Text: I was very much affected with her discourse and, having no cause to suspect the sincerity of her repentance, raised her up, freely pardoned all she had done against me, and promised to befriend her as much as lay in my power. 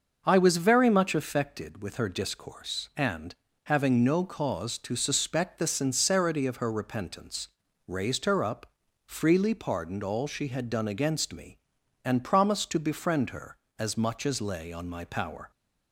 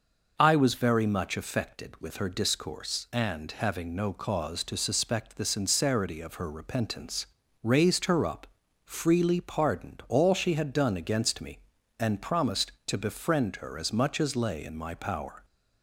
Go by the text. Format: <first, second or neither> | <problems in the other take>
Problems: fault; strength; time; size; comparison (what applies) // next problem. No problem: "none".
second | starts louder than the rest; noticeable; until 1.2 s; 6 dB // says "on" for "in"; at 14.7 s